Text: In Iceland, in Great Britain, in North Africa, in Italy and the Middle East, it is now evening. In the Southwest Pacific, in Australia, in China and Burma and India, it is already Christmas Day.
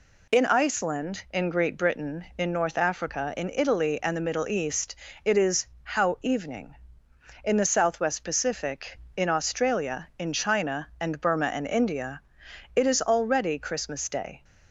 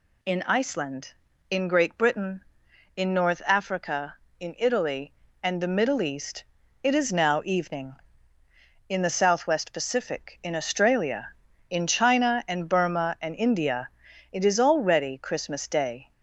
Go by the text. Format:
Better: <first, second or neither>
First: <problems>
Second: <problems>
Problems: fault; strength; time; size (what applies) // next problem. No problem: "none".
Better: second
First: says "how" for "now"; at 5.8 s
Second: none